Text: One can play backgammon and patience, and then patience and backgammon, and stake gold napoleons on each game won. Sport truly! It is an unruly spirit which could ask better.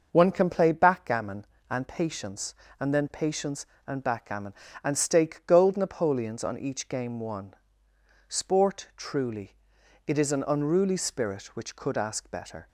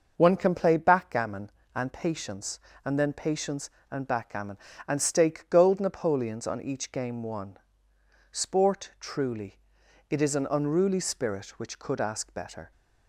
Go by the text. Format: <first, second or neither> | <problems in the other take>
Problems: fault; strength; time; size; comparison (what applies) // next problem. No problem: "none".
neither | starts louder than the rest; noticeable; the same in both